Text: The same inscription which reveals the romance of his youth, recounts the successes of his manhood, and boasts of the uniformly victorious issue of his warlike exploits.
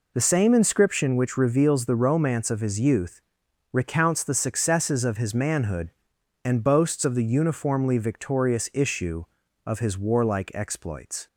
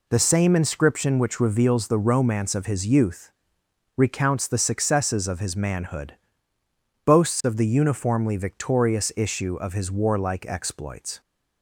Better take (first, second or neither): first